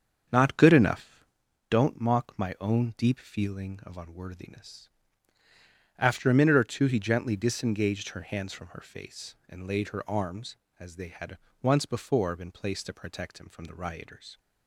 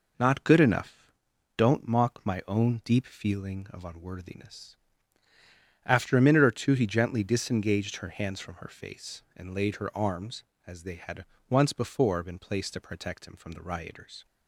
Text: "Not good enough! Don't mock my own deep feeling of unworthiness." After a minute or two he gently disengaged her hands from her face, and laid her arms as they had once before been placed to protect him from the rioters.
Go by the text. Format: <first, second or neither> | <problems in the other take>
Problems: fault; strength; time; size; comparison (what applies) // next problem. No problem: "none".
second | starts louder than the rest; strong; until 1.5 s; 7.5 dB // pauses between "had" and "once"; slight; at 11.3 s; 0.24 s long; slight in the second